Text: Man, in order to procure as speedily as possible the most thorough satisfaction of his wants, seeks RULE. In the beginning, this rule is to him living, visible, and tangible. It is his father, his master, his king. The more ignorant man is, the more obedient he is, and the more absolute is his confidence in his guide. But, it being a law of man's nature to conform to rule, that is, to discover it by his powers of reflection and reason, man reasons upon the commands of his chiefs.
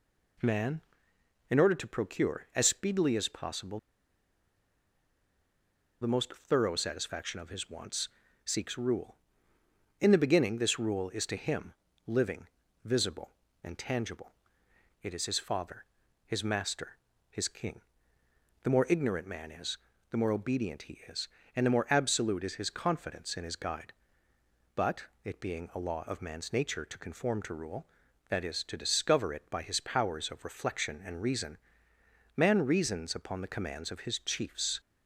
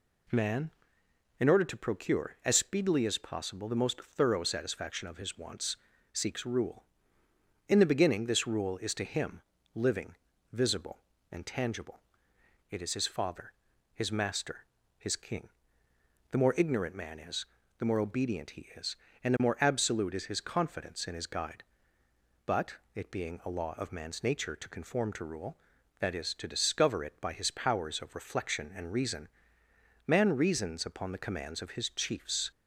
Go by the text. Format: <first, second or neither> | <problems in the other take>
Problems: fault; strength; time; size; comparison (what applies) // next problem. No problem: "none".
second | pauses between "possible" and "the"; strong; at 3.7 s; 2.2 s long // pauses between "him" and "living"; slight; at 11.7 s; 0.34 s long; slight in the second